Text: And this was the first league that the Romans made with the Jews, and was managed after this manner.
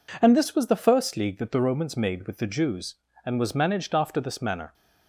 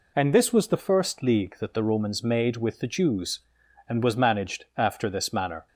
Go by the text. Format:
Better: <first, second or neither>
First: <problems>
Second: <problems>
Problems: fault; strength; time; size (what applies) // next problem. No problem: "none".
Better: neither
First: none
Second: none